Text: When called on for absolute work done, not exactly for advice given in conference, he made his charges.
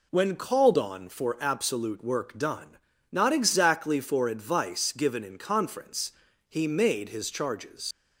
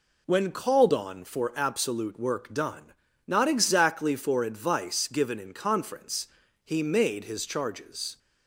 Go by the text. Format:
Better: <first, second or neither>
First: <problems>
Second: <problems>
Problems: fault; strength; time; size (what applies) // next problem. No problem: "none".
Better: second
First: leaves "charges" unfinished; at 7.9 s; 120 ms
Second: none